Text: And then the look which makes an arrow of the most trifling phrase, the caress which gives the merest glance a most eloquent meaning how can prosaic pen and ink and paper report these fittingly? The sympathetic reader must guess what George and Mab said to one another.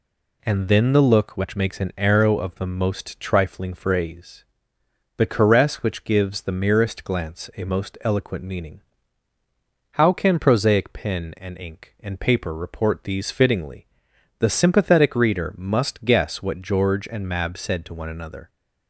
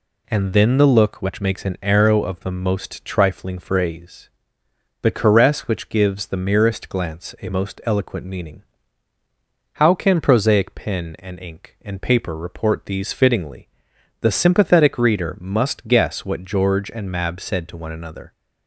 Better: neither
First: pauses between "meaning" and "how"; at 8.7 s; 1.1 s long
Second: pauses between "meaning" and "how"; at 8.6 s; 1.1 s long

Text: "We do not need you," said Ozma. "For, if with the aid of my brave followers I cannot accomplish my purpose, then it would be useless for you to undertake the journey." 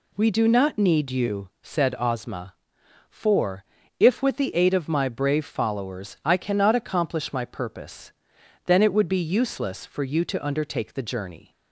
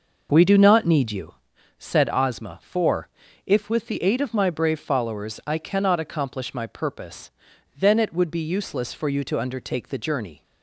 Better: first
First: none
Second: starts louder than the rest; noticeable; until 1.6 s; 6 dB

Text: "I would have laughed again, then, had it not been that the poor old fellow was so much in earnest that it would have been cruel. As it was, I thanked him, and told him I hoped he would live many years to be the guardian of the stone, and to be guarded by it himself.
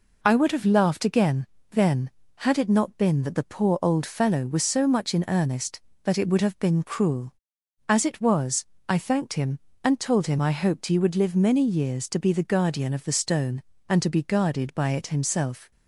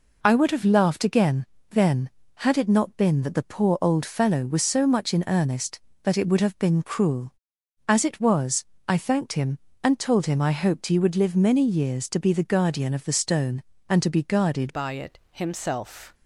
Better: first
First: none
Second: changes voice at "by"; from 14.7 s on; 1.4 s long

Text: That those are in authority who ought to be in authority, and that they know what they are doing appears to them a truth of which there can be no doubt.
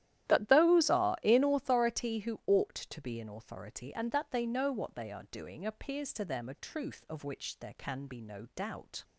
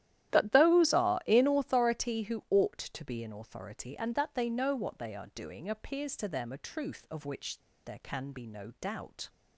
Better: first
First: starts louder than the rest; strong; until 1.3 s; 12.5 dB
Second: starts louder than the rest; strong; until 1.3 s; 12.5 dB // pauses between "which" and "there"; slight; at 7.5 s; 0.25 s long

